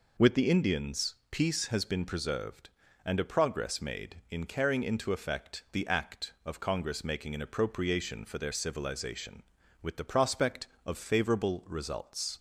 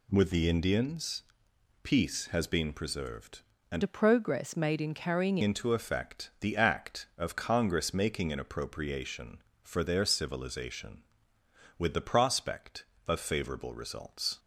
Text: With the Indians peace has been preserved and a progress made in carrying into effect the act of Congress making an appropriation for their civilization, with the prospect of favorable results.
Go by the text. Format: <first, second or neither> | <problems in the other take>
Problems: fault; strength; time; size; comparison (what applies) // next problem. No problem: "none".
first | pauses between "Indians" and "peace"; noticeable; at 1.2 s; 0.62 s long; slight in the first // changes voice from "a" to "carrying"; from 3.8 to 5.3 s; 1.5 s long